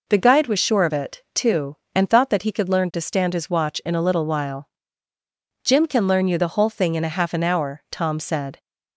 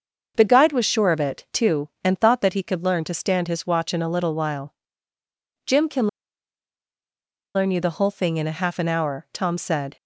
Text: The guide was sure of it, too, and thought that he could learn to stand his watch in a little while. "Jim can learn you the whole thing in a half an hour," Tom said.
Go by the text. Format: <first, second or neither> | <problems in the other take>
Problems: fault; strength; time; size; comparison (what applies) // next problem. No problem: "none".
first | starts louder than the rest; until 1.3 s; 6.5 dB // pauses between "can" and "learn"; strong; at 6.0 s; 1.4 s long